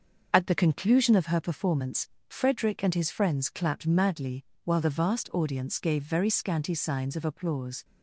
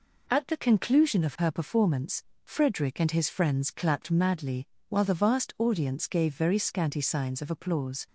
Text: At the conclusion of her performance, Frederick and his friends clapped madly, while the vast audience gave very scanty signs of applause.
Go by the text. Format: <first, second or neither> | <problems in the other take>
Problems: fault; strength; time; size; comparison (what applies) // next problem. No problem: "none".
second | starts louder than the rest; until 1.4 s; 6 dB